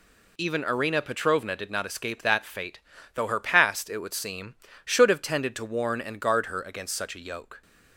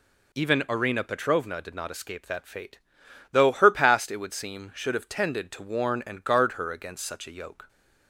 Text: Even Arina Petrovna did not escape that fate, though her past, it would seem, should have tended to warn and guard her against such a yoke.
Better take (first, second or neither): neither